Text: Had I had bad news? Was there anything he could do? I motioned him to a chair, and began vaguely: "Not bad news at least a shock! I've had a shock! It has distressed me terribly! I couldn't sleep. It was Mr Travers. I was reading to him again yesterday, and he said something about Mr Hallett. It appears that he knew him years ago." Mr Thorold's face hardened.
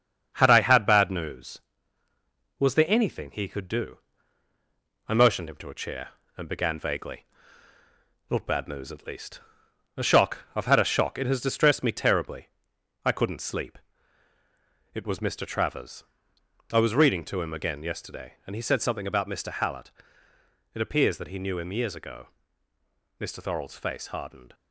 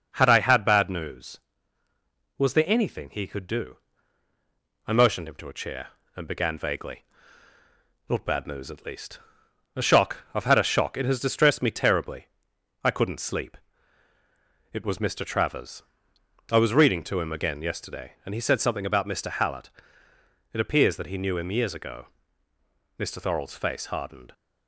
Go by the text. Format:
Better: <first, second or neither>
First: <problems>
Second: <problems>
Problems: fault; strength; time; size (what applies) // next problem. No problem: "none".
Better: second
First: gets quieter; throughout; 3.5 dB // pauses between "least" and "a"; noticeable; at 9.3 s; 0.58 s long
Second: pauses between "least" and "a"; noticeable; at 9.1 s; 0.58 s long